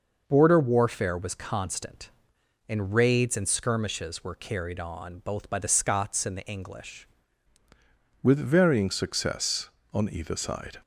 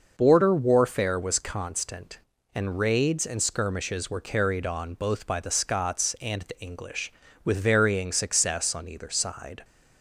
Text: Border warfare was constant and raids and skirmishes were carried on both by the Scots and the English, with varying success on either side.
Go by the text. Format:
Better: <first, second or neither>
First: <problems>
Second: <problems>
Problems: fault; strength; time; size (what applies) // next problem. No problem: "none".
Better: second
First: changes voice at "with"; from 8.2 s on; 2.5 s long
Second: none